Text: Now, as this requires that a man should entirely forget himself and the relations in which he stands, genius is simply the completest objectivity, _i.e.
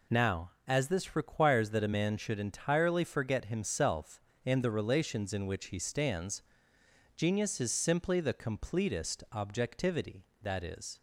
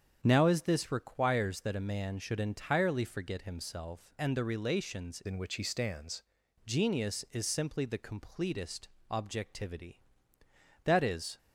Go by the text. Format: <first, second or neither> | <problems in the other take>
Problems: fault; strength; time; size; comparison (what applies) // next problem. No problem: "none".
first | starts louder than the rest; strong; until 1.2 s; 8 dB // changes voice from "in" to "stands"; from 5.2 to 6.2 s; 1.0 s long // pauses between "completest" and "objectivity"; slight; at 8.8 s; 0.22 s long